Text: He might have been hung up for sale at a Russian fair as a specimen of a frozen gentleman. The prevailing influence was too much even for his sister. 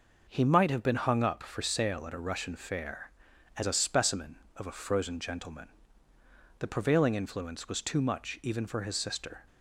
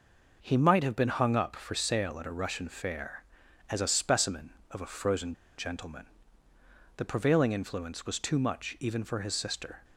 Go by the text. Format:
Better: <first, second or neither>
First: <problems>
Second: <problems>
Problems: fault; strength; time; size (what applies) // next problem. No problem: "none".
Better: first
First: none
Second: pauses between "frozen" and "gentleman"; slight; at 5.3 s; 0.23 s long